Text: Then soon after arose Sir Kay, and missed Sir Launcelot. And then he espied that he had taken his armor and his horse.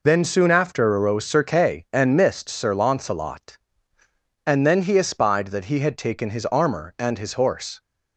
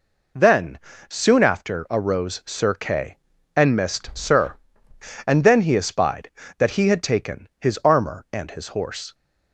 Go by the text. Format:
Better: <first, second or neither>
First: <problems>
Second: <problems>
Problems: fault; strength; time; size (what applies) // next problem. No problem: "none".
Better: first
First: none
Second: pauses between "Then" and "soon"; slight; at 0.7 s; 0.30 s long // skips "Launcelot"; at 4.9 s